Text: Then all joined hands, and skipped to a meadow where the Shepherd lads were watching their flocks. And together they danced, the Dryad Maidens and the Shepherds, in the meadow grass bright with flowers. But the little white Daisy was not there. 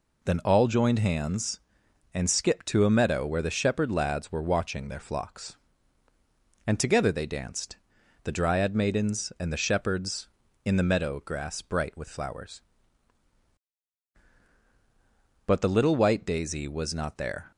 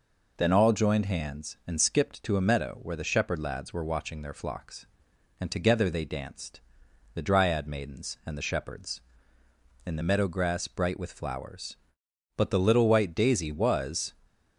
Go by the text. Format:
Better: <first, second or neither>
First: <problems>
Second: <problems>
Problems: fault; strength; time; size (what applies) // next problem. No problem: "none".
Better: first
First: none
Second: stops before "not there"; at 14.2 s